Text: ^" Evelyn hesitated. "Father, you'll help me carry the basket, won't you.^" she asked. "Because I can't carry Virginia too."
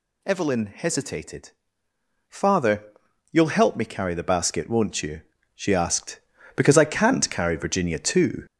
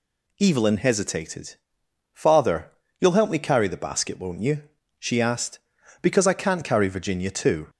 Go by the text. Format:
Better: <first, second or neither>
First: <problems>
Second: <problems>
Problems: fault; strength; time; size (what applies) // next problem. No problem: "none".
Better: second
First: gets louder; noticeable; throughout; 5.5 dB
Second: none